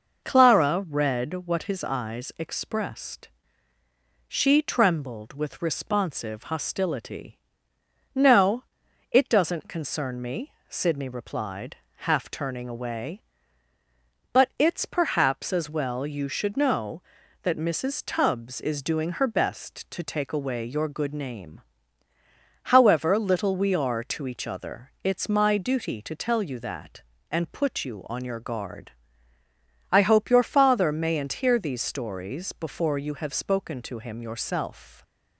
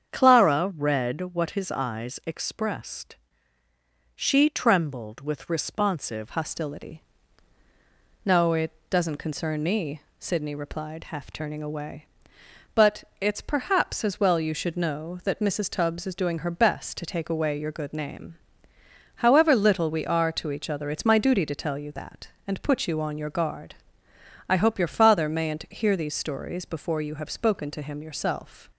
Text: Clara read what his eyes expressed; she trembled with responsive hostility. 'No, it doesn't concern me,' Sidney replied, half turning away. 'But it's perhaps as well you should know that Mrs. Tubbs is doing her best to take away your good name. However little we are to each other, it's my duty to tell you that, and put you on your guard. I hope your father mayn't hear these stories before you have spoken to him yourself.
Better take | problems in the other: first | starts louder than the rest; strong; until 1.1 s; 7.5 dB // changes voice at "hostility"; from 6.2 s on; 22.4 s long // pauses between "it" and "doesn't"; slight; at 8.6 s; 0.22 s long

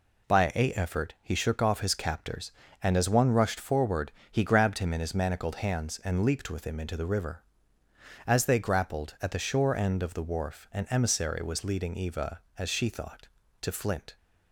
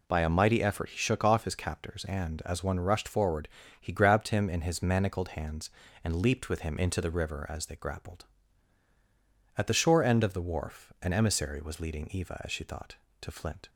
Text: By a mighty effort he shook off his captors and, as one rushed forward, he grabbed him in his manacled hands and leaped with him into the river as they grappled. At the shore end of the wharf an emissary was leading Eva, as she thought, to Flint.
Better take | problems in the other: second | skips "mighty"; at 0.7 s

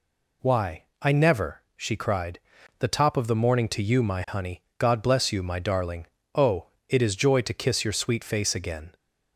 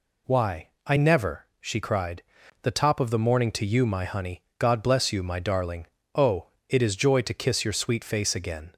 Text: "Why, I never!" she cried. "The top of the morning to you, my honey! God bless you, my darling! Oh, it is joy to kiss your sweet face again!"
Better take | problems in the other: neither | none

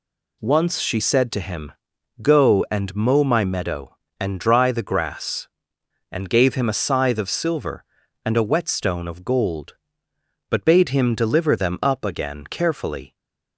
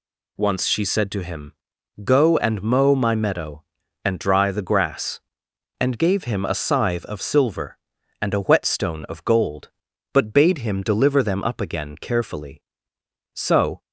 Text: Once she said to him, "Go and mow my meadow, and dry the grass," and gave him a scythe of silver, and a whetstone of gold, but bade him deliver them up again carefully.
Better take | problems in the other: first | goes on to say "So"; slight; from 13.3 s on; 0.48 s long

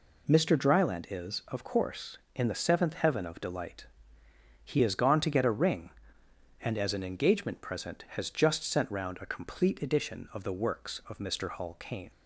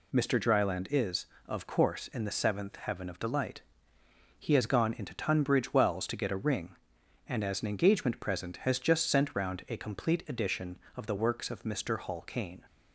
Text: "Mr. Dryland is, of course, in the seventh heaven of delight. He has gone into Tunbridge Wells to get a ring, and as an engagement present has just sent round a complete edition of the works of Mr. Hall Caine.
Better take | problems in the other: second | skips "into Tunbridge Wells"; at 5.1 s

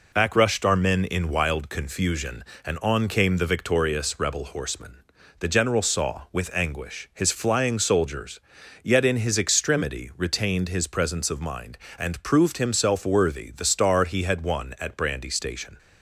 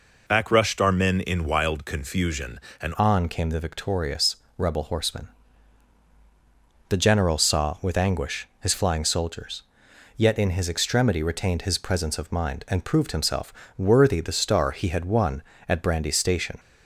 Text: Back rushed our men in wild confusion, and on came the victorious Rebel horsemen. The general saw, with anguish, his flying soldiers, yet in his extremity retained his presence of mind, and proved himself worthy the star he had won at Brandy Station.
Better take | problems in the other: first | changes voice at "on"; from 2.9 s on; 13.6 s long // pauses between "victorious" and "Rebel"; slight; at 4.3 s; 0.22 s long // pauses between "himself" and "worthy"; slight; at 13.5 s; 0.26 s long

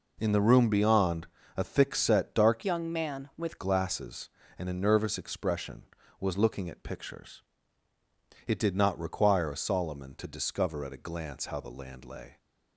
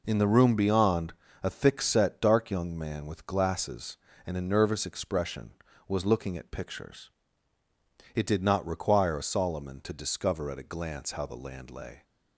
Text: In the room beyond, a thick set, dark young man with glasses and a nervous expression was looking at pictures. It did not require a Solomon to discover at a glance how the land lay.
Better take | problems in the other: second | changes voice from "young" to "with"; from 2.6 to 3.5 s; 0.9 s long

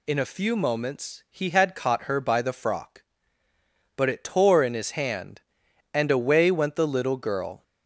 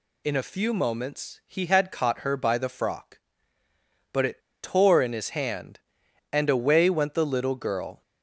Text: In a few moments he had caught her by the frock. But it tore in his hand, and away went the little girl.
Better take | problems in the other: first | pauses between "it" and "tore"; slight; at 4.4 s; 0.22 s long

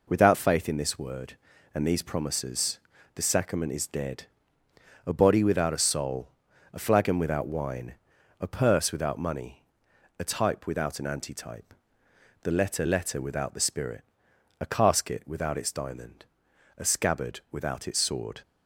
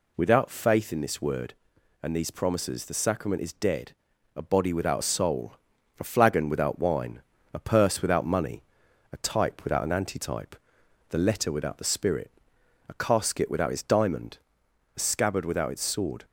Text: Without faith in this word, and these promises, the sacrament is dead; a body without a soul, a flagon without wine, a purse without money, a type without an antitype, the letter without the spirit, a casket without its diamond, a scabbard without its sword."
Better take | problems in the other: second | says "letter" twice; at 12.8 s

